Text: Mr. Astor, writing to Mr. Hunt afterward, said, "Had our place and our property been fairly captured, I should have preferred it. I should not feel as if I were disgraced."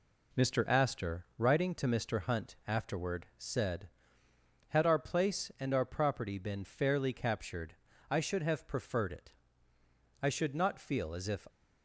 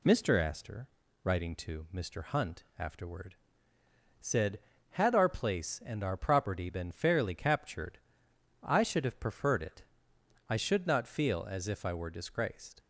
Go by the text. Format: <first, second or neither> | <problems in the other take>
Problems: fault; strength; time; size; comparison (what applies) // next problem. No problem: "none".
second | stops before "I were disgraced"; at 11.4 s